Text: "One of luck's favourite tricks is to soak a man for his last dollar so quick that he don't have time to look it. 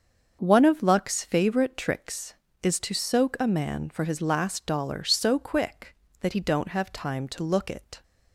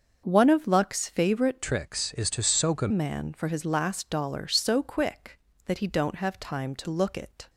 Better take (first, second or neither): first